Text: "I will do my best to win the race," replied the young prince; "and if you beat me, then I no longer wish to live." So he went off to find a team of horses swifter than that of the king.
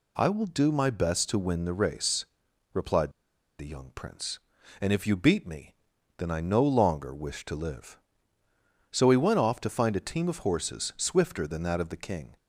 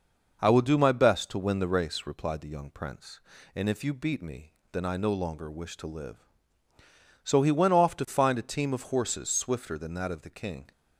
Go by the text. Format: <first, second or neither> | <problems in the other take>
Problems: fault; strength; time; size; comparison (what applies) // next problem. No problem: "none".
second | pauses between "replied" and "the"; noticeable; at 3.1 s; 0.48 s long